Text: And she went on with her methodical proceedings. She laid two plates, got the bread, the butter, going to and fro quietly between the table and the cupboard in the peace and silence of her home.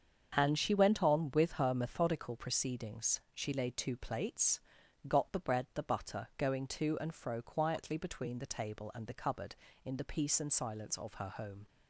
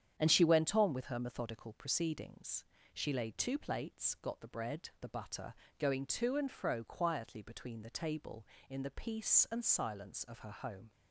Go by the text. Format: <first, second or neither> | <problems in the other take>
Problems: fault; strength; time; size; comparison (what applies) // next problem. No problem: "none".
first | starts louder than the rest; strong; until 1.1 s; 9 dB; also in the first // skips "and the cupboard"; at 8.5 s